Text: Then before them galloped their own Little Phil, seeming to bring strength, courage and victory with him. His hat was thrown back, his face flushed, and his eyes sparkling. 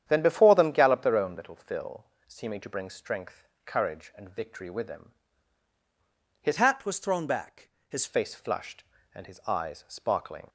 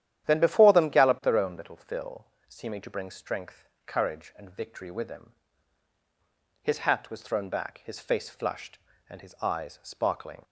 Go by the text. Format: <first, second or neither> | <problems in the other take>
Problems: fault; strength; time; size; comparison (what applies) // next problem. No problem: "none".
second | starts louder than the rest; strong; until 1.0 s; 9.5 dB; strong in the second // changes voice from "hat" to "his"; from 6.5 to 8.0 s; 1.5 s long